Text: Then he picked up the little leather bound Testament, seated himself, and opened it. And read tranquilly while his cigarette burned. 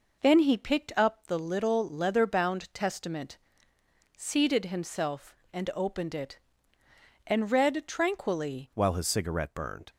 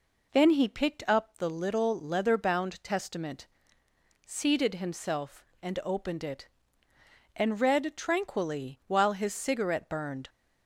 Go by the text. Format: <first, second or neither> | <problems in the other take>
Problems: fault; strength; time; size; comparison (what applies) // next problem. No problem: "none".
second | changes voice at "while"; from 8.7 s on; 1.1 s long